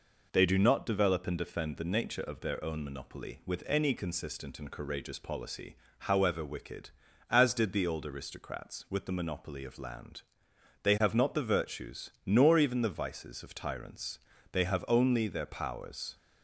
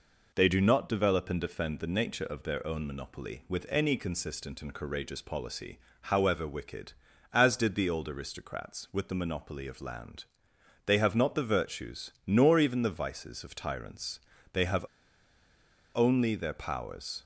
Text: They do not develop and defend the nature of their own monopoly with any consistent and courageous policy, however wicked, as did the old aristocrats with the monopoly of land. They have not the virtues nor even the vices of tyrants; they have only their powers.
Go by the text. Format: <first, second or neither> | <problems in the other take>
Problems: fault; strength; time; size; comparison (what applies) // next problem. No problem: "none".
first | pauses between "have" and "only"; at 14.8 s; 1.0 s long